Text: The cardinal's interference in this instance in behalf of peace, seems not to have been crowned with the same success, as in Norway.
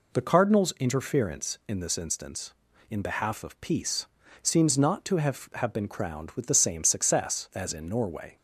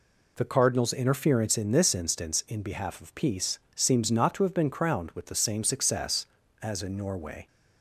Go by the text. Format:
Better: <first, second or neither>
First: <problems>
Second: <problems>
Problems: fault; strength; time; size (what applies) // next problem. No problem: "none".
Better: second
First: says "have" twice; at 5.5 s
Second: none